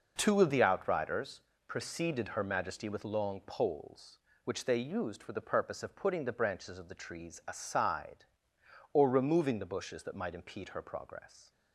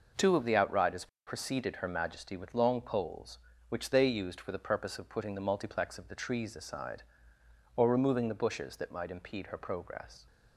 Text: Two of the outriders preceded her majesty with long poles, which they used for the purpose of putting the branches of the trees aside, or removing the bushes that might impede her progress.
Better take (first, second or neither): first